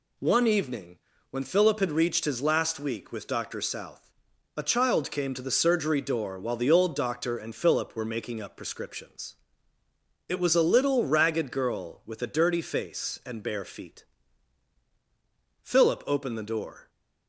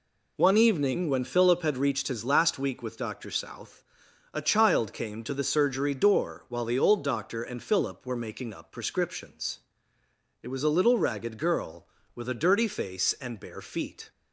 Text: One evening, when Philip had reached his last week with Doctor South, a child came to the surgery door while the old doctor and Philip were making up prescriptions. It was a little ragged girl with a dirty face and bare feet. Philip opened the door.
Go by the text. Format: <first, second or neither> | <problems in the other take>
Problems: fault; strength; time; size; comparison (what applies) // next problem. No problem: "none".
first | stops before "Philip opened the door"; at 14.1 s